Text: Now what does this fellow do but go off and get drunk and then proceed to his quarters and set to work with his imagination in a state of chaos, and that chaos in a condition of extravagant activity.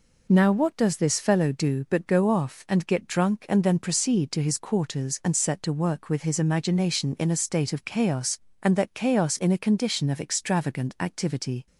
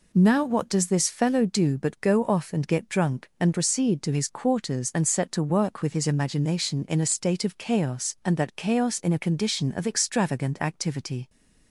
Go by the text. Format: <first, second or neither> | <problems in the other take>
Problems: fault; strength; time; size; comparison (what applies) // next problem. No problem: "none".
first | skips "then"; at 3.5 s